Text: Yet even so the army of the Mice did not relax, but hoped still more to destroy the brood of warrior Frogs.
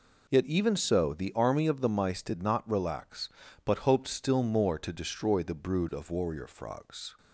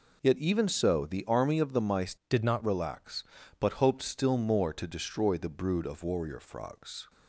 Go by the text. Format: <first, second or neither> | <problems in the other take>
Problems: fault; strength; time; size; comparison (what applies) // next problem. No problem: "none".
first | changes voice from "did" to "not"; from 2.2 to 2.6 s; 0.4 s long